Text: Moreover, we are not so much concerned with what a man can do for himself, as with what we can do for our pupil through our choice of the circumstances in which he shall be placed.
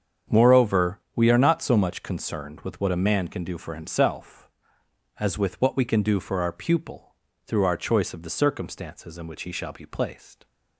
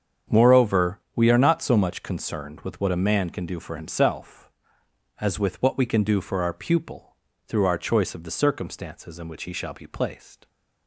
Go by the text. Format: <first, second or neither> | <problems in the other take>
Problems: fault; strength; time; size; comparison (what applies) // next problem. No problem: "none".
neither | starts louder than the rest; strong; the same in both // pauses between "pupil" and "through"; slight; the same in both